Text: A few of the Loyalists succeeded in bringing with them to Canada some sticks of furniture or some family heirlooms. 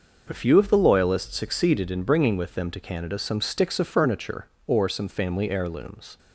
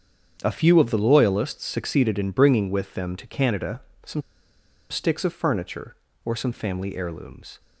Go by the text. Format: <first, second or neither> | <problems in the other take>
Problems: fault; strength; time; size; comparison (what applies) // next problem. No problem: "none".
first | starts louder than the rest; strong; until 1.4 s; 8 dB // pauses between "Canada" and "some"; slight; at 3.8 s; 0.24 s long // pauses between "some" and "sticks"; noticeable; at 4.2 s; 0.68 s long